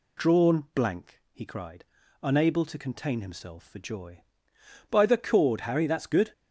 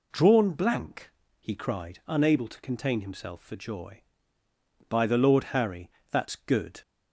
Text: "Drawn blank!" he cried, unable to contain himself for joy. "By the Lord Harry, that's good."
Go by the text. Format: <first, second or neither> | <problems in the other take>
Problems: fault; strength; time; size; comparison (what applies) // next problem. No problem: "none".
second | says "Cord" for "Lord"; at 5.1 s